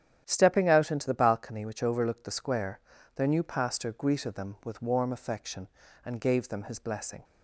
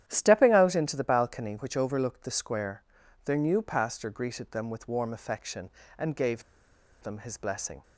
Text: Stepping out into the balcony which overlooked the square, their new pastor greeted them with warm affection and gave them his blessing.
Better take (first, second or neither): first